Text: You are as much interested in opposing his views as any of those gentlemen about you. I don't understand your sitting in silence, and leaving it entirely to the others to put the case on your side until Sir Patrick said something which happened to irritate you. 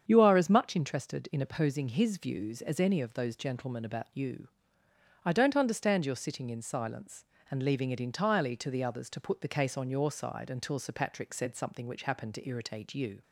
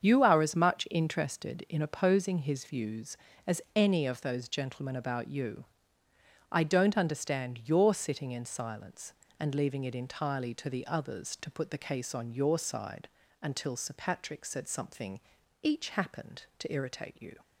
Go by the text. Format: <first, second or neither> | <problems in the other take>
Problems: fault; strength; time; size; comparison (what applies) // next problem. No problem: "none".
first | starts louder than the rest; strong; until 1.0 s; 7 dB; strong in the first // pauses between "side" and "until"; slight; at 13.0 s; 0.34 s long // says "each" for "which"; at 15.6 s